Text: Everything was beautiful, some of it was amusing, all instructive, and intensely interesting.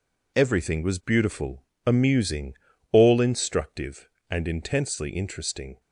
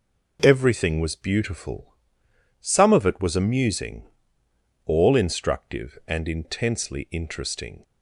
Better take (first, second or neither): second